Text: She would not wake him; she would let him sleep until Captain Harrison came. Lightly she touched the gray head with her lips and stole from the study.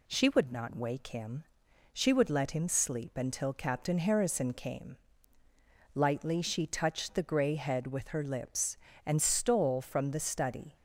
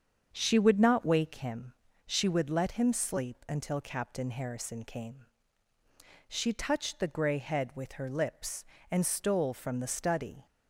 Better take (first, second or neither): first